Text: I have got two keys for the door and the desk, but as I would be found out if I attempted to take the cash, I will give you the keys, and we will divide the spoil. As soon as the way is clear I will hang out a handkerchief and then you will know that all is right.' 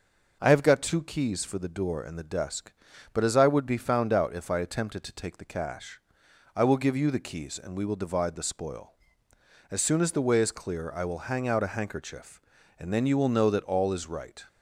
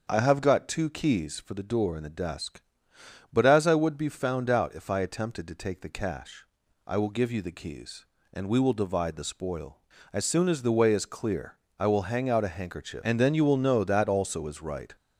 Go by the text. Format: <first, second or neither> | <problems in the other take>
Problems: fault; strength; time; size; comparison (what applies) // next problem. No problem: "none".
first | starts louder than the rest; until 1.1 s; 6.5 dB // pauses between "clear" and "I"; slight; at 11.5 s; 0.22 s long // says "also" for "all"; at 14.0 s